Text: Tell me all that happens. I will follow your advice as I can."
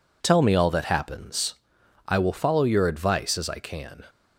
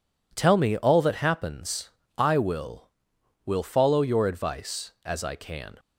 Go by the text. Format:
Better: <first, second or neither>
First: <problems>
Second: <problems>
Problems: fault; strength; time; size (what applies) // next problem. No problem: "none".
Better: first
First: none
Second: says "will" twice; at 3.4 s